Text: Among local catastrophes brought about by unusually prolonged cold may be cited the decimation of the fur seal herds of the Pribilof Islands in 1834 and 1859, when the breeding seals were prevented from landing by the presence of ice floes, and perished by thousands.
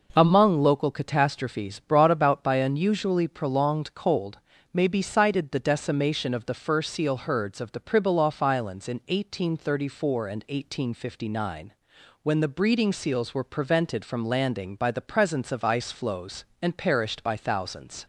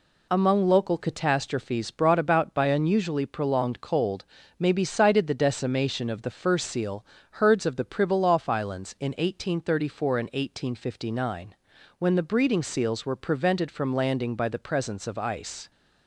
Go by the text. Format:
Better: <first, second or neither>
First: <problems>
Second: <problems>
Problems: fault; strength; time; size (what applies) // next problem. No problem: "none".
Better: first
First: pauses between "cold" and "may"; slight; at 4.3 s; 0.34 s long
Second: pauses between "cold" and "may"; slight; at 4.2 s; 0.32 s long // pauses between "seal" and "herds"; slight; at 7.0 s; 0.28 s long // stops before "floes and perished by thousands"; at 15.7 s